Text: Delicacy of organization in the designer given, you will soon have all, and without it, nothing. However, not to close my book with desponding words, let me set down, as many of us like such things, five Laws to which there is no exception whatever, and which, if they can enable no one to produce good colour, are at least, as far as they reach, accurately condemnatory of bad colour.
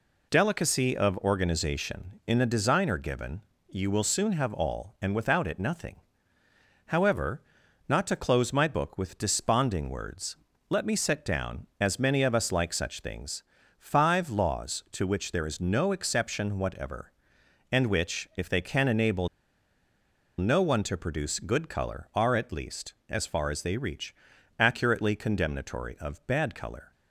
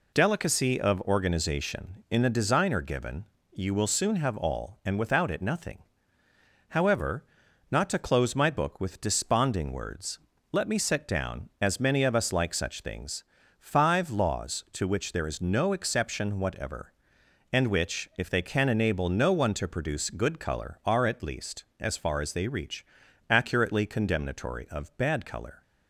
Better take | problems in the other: second | pauses between "enable" and "no"; at 19.2 s; 1.1 s long

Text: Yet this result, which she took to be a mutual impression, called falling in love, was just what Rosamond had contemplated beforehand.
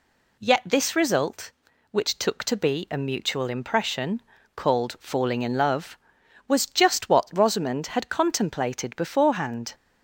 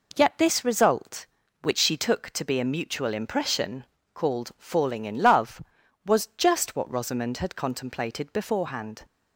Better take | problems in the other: second | skips "she"; at 2.1 s

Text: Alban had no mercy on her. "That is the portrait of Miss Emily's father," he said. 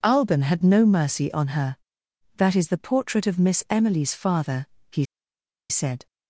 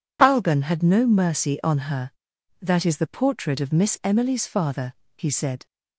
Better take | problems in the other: second | pauses between "he" and "said"; noticeable; at 5.0 s; 0.66 s long

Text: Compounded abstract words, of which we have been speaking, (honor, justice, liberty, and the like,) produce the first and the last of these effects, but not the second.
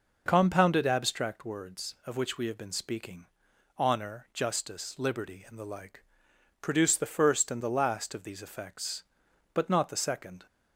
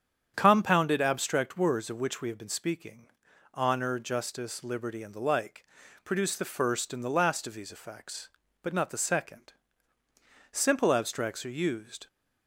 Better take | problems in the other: first | starts louder than the rest; strong; until 1.3 s; 8.5 dB // goes on to say "Simple abstracts are used"; from 10.5 s on; 1.5 s long

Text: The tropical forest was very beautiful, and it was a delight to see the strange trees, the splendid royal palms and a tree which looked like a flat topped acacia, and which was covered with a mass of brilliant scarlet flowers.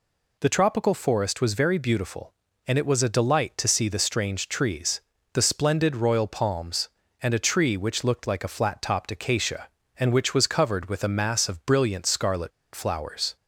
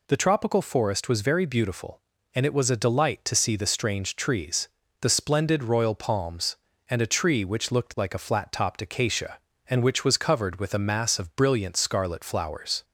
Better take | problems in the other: second | pauses between "scarlet" and "flowers"; slight; at 12.5 s; 0.24 s long

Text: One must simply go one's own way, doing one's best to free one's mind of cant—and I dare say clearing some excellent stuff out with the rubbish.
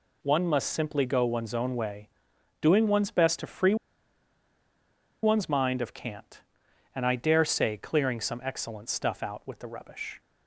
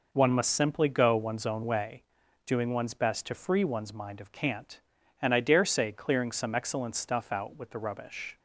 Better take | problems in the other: second | pauses between "free" and "one's"; strong; at 3.7 s; 1.4 s long

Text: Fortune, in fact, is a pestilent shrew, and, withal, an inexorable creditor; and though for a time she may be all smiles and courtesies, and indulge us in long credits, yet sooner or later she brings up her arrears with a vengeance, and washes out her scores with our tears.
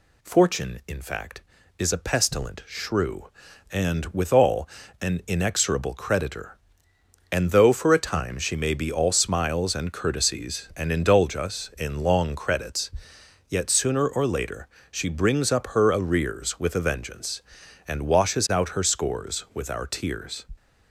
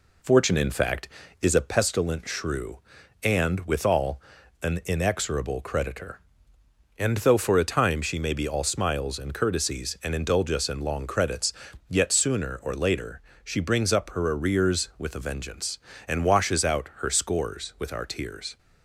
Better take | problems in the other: first | starts louder than the rest; slight; until 1.9 s; 3 dB // pauses between "later" and "she"; slight; at 13.1 s; 0.24 s long; slight in the first

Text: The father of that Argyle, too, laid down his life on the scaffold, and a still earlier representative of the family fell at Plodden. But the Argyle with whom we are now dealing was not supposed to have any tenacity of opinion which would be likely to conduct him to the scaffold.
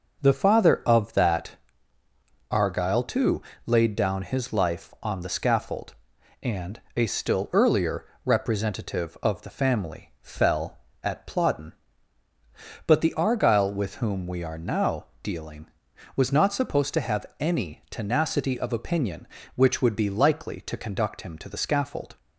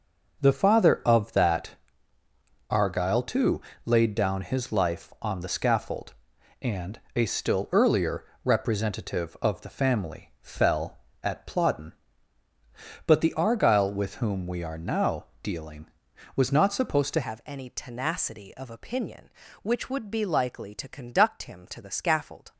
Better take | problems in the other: first | pauses between "that" and "Argyle"; noticeable; at 1.7 s; 0.98 s long; noticeable in the first // pauses between "and" and "a"; slight; at 6.9 s; 0.16 s long; slight in the first // pauses between "earlier" and "representative"; slight; at 8.2 s; 0.22 s long; slight in the first // pauses between "now" and "dealing"; slight; at 15.2 s; 0.18 s long; slight in the first // changes voice at "have"; from 17.2 s on; 5.3 s long

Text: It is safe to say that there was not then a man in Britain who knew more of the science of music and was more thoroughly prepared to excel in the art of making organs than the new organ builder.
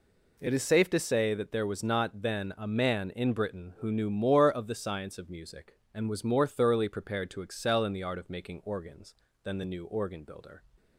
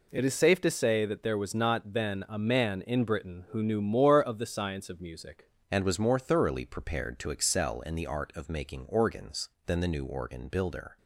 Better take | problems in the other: first | changes voice at "and"; from 5.7 s on; 5.2 s long

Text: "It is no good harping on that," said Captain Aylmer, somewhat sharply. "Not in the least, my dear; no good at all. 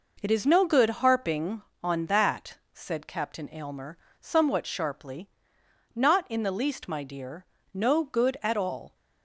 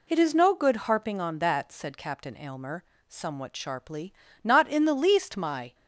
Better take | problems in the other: first | stops before "dear no good at all"; at 5.7 s

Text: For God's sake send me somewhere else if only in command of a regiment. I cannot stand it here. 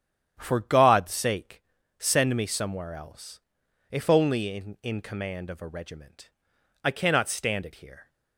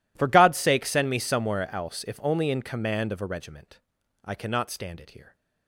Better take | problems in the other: second | starts louder than the rest; strong; until 1.3 s; 9.5 dB // pauses between "sake" and "send"; at 1.6 s; 0.38 s long // pauses between "else" and "if"; noticeable; at 3.3 s; 0.50 s long // says "in" twice; at 4.8 s

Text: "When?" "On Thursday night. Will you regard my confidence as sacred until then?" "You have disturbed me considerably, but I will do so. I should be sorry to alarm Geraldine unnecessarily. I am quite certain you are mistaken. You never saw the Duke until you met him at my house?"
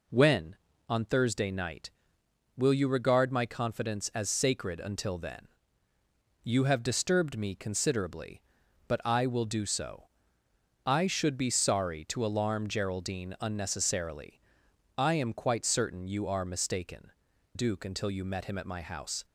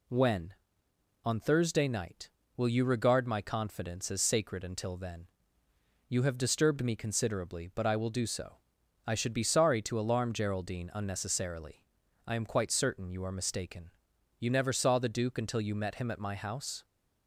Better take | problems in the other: second | skips "You never saw the"; at 17.3 s

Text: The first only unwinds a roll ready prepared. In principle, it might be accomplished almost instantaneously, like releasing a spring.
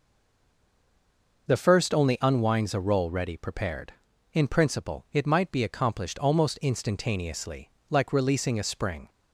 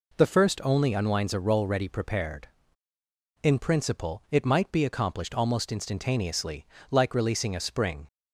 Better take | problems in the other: second | stays silent before the first word; noticeable; until 1.4 s; 1.4 s long

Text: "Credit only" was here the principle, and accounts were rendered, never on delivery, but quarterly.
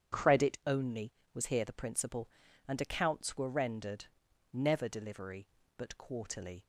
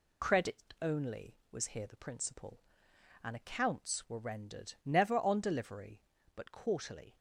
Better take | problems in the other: second | starts louder than the rest; strong; until 1.4 s; 8.5 dB // skips "on"; at 4.8 s

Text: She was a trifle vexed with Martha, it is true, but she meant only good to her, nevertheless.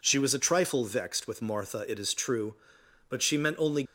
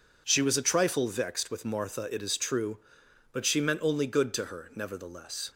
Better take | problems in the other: second | stops before "good to her nevertheless"; at 3.8 s

